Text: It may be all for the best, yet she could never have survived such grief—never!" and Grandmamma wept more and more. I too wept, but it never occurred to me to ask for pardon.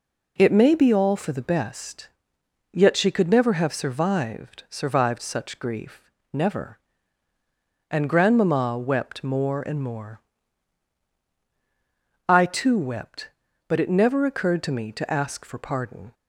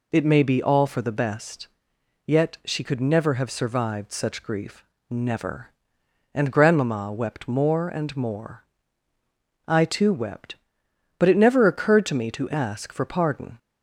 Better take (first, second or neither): second